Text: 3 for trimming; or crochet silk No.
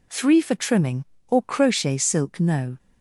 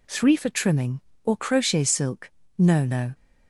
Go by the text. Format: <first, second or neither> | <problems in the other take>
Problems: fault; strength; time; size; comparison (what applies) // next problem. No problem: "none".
first | pauses between "silk" and "No"; slight; at 2.2 s; 0.28 s long // says "No" twice; at 2.8 s